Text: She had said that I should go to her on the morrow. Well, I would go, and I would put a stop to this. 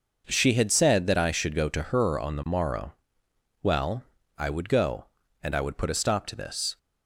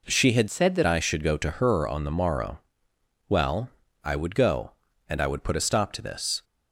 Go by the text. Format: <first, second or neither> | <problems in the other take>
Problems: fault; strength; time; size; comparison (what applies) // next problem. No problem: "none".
first | changes voice from "said" to "that"; from 0.5 to 0.8 s; 0.3 s long